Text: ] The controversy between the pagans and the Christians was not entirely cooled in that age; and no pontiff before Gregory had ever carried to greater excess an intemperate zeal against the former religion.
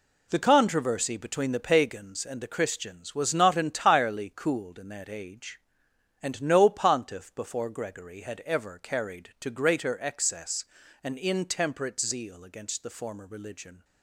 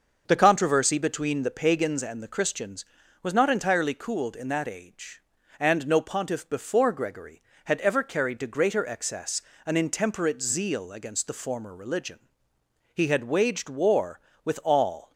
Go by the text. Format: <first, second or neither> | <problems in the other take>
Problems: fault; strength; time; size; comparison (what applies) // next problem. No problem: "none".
first | starts louder than the rest; noticeable; until 1.2 s; 6 dB // pauses between "excess" and "an"; slight; at 9.4 s; 0.26 s long; slight in the first // goes on to say "He had waged war with all"; strong; from 12.9 s on; 2.2 s long